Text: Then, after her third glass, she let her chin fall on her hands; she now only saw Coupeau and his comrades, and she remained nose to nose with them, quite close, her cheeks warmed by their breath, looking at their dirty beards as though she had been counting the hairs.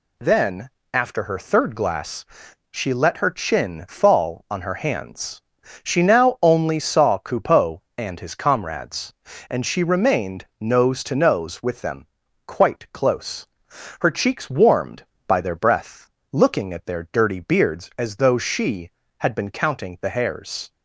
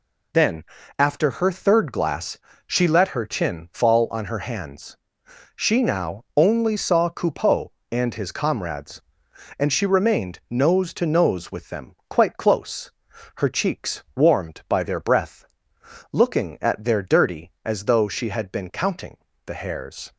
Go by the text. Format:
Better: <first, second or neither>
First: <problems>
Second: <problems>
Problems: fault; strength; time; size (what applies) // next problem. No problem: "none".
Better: first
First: none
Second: skips "beards"; at 17.5 s // pauses between "counting" and "the"; slight; at 19.1 s; 0.30 s long